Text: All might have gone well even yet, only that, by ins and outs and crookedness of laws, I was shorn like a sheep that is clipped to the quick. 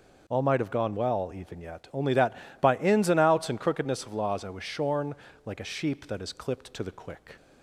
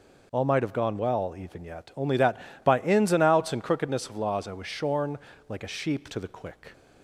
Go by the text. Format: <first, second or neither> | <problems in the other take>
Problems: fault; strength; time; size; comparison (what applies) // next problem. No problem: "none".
first | pauses between "shorn" and "like"; slight; at 5.1 s; 0.30 s long; slight in the first // skips "that is clipped"; at 6.1 s